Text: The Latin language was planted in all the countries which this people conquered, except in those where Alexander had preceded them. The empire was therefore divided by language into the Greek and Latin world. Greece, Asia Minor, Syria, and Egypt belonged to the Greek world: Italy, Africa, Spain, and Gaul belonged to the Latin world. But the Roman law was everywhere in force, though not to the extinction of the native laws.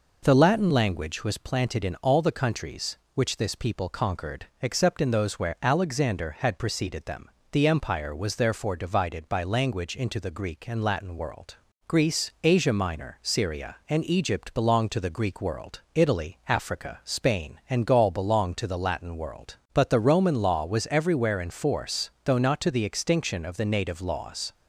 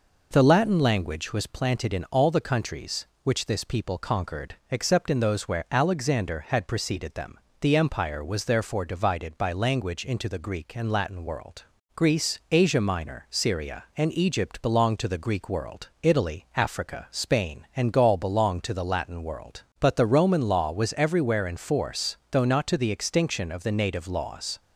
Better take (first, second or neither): neither